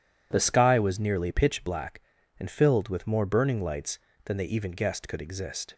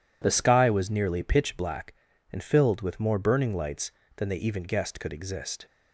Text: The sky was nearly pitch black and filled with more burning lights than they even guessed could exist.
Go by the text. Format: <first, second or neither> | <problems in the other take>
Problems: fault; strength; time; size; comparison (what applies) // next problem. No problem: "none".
neither | none